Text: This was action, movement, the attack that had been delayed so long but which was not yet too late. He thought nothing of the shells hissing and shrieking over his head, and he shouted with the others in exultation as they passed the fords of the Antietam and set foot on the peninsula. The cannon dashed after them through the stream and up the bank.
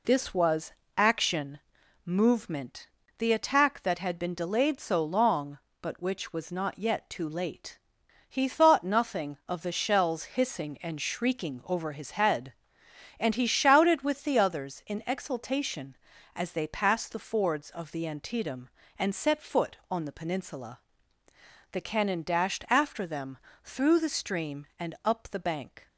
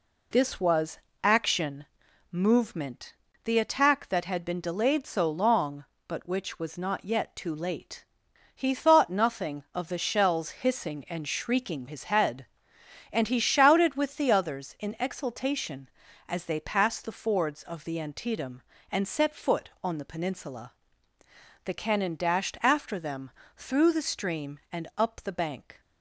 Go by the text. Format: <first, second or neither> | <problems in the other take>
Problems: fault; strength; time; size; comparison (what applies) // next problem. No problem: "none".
first | pauses between "was" and "action"; slight; at 0.9 s; 0.24 s long; slight in the first // skips "over"; at 11.8 s // pauses between "them" and "through"; slight; at 23.3 s; 0.26 s long; slight in the first